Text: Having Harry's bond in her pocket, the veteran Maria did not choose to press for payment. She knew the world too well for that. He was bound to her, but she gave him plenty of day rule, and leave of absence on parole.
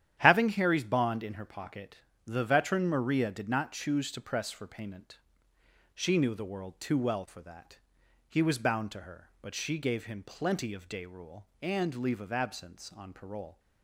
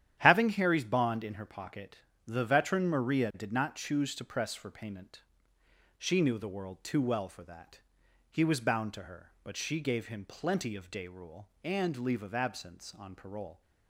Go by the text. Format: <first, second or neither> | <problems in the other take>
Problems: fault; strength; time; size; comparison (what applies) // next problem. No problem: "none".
neither | starts louder than the rest; strong; the same in both